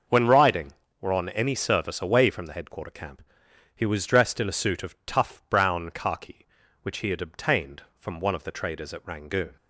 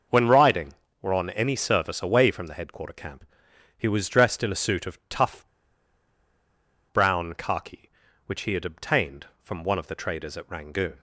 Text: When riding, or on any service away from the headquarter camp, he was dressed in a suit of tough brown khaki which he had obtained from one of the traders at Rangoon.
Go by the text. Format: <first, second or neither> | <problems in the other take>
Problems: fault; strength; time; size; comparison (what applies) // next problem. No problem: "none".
first | starts louder than the rest; noticeable; until 1.4 s; 6 dB; noticeable in the first // pauses between "tough" and "brown"; strong; at 5.4 s; 1.4 s long